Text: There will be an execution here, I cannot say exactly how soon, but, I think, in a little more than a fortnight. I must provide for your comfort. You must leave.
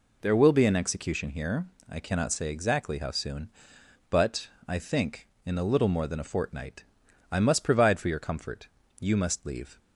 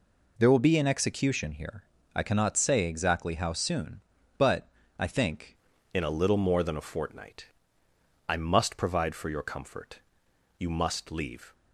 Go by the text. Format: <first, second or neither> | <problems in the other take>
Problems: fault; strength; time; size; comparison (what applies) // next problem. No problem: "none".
first | changes voice at "in"; from 5.9 s on; 5.6 s long